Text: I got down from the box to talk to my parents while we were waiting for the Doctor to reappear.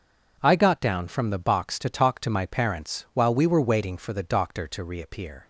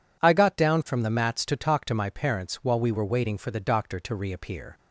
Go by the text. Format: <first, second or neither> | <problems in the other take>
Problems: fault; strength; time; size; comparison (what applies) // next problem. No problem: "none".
first | says "mats" for "box"; at 1.0 s